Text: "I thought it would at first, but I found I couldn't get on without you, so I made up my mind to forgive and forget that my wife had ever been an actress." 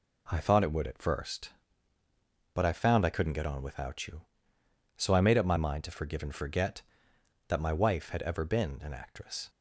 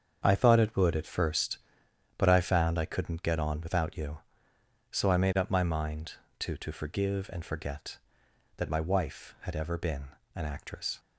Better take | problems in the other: first | starts louder than the rest; strong; until 1.2 s; 7.5 dB // says "to" twice; at 6.5 s // pauses between "been" and "an"; slight; at 10.0 s; 0.26 s long

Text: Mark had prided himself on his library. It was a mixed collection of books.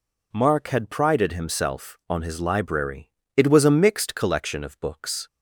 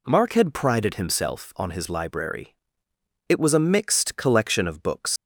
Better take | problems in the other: first | leaves "books" unfinished; at 5.1 s; 100 ms

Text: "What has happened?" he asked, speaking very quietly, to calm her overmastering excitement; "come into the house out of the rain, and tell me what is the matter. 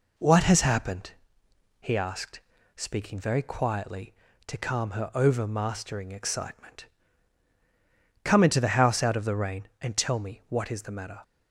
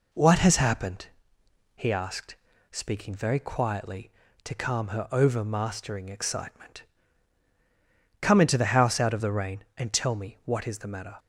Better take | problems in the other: neither | none

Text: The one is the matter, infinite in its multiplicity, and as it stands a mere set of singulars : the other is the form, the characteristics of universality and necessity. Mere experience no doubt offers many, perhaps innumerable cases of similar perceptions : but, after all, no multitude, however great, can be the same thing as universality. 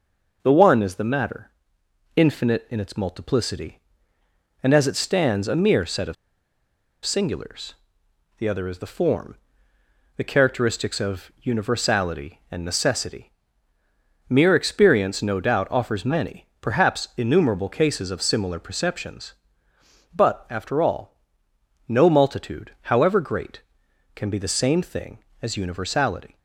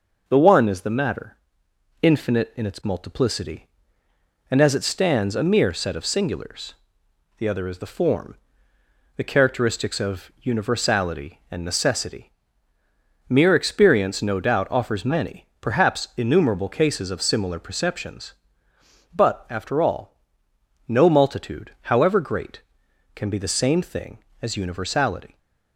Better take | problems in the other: second | pauses between "of" and "singulars"; noticeable; at 6.1 s; 0.90 s long

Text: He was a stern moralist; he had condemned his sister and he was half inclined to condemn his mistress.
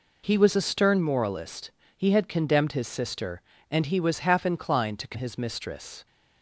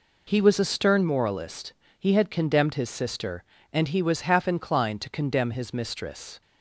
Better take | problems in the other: second | skips "condemn"; at 5.1 s

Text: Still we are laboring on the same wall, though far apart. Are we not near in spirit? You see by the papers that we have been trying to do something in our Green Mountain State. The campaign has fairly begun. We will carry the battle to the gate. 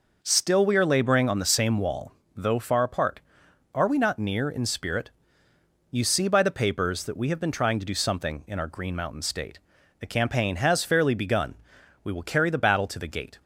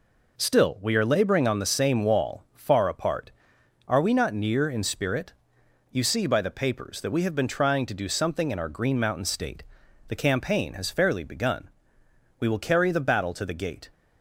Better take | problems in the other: first | skips "though"; at 2.4 s

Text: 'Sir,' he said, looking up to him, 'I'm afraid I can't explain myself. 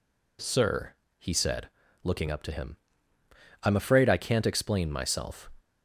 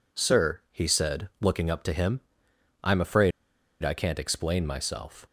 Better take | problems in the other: first | pauses between "afraid" and "I"; noticeable; at 3.3 s; 0.52 s long

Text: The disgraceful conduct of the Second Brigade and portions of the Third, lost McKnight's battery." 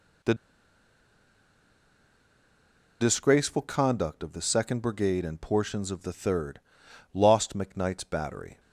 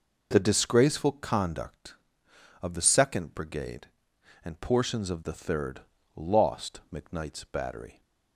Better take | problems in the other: second | pauses between "The" and "disgraceful"; strong; at 0.3 s; 2.6 s long

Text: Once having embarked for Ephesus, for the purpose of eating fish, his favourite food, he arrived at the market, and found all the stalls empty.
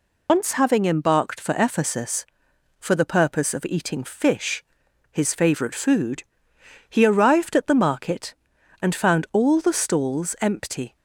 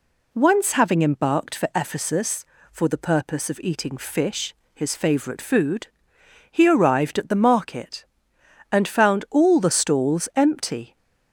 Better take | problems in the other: second | loses the start of "Once"; at 0.2 s; 80 ms

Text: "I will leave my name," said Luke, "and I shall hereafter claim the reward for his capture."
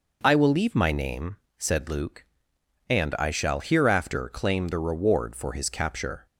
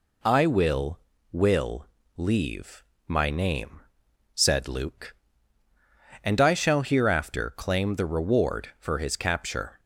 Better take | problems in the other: first | says "will" twice; at 1.3 s // pauses between "leave" and "my"; slight; at 2.8 s; 0.24 s long

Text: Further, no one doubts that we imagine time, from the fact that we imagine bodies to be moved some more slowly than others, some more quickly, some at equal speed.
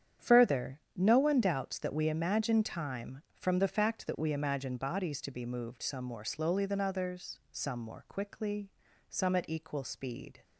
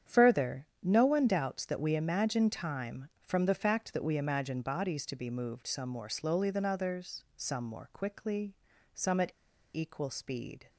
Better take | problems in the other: first | starts louder than the rest; strong; until 1.2 s; 8.5 dB; strong in the first // pauses between "at" and "equal"; at 9.3 s; 0.42 s long

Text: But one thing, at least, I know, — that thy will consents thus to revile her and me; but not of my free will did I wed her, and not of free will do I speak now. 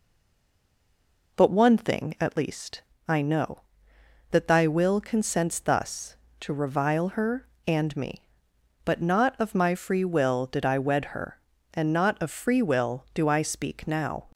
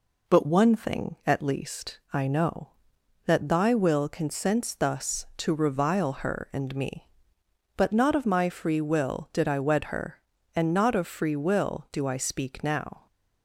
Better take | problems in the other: second | stays silent before the first word; noticeable; until 1.3 s; 1.3 s long

